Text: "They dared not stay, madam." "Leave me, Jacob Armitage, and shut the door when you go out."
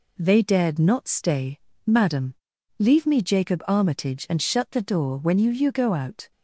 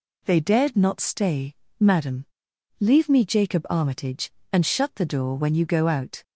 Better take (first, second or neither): second